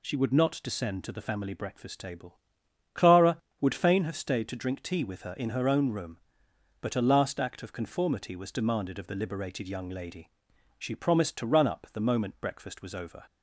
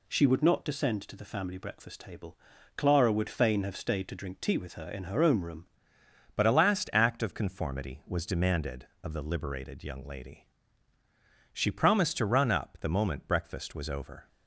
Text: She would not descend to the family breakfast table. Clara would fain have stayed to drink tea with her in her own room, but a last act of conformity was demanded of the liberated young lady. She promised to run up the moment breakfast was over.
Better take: first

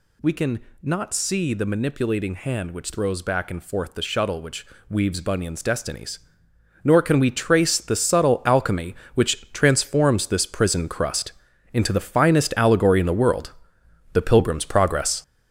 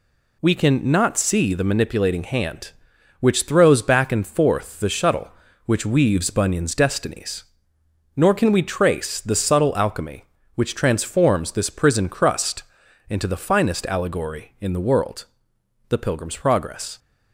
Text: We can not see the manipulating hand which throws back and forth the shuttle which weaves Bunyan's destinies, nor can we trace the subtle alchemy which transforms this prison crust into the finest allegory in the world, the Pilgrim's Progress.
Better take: second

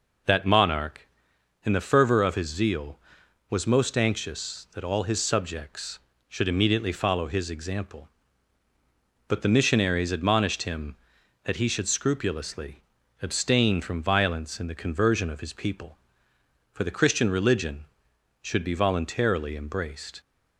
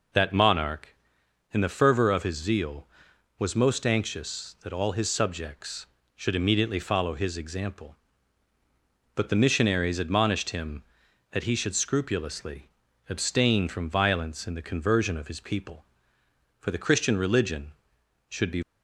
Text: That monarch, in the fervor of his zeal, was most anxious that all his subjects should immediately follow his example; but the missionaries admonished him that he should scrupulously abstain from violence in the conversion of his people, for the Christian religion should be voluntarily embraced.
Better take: first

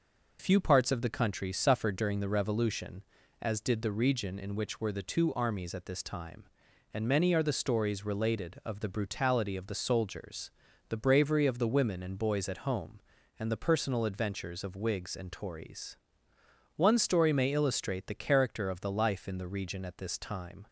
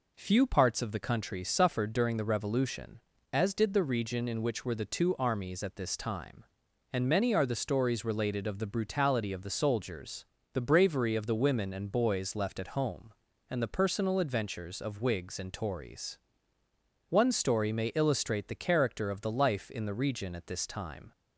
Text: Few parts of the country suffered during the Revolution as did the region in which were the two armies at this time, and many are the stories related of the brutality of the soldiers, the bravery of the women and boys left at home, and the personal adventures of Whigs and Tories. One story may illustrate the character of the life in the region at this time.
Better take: second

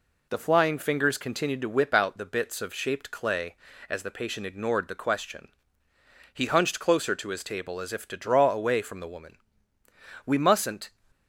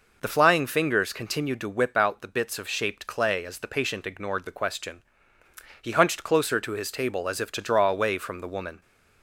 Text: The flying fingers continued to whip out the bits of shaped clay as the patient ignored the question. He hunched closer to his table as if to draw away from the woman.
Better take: second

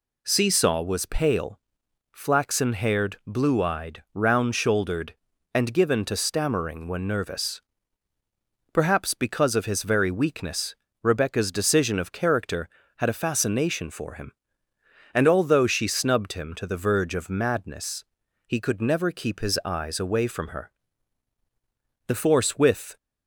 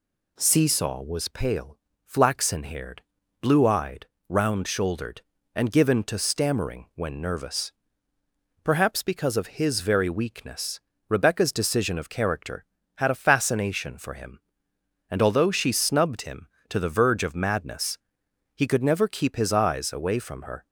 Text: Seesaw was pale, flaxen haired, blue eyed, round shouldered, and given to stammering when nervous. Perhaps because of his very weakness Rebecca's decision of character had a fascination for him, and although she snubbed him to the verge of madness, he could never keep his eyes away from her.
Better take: second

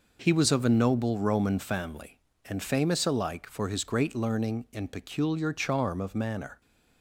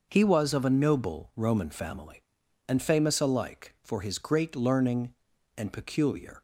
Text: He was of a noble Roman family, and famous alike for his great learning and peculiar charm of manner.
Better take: first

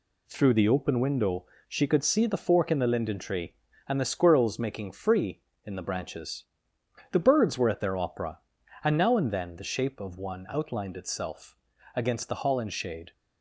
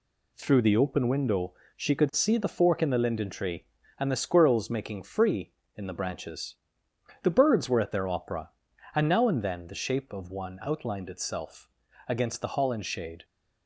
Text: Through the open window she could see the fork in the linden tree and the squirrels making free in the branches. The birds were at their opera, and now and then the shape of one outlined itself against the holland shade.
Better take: neither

